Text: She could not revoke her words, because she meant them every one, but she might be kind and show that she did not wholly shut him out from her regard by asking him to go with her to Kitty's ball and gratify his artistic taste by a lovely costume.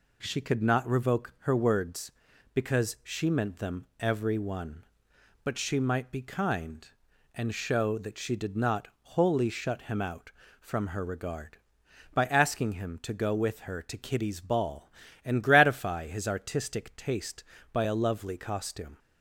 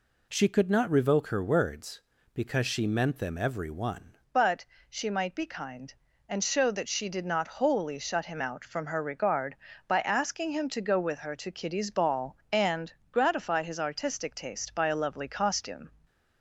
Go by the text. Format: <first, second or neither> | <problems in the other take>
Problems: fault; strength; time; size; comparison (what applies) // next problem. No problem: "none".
first | changes voice at "but"; from 4.3 s on; 11.5 s long // pauses between "but" and "she"; slight; at 4.6 s; 0.24 s long // pauses between "and" and "gratify"; slight; at 12.9 s; 0.18 s long